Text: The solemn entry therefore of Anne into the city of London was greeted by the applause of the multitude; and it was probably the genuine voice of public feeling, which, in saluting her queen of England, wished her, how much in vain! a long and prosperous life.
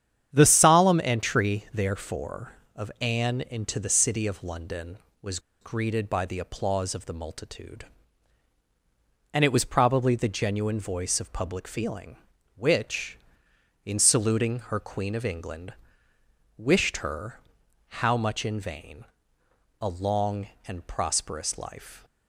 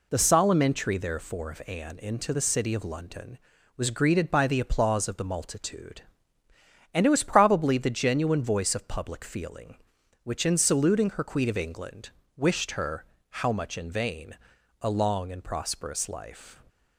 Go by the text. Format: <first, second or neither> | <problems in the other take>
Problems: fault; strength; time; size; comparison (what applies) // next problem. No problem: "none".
second | starts louder than the rest; strong; until 1.3 s; 9.5 dB // pauses between "was" and "greeted"; slight; at 5.3 s; 0.22 s long